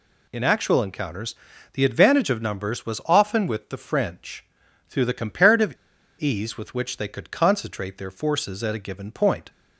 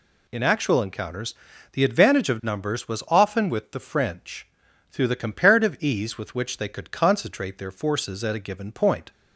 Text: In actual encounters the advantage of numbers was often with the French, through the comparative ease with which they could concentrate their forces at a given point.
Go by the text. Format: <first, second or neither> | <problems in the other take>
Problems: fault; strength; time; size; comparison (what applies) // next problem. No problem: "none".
second | pauses between "encounters" and "the"; slight; at 1.3 s; 0.36 s long; slight in the second // pauses between "comparative" and "ease"; at 5.7 s; 0.45 s long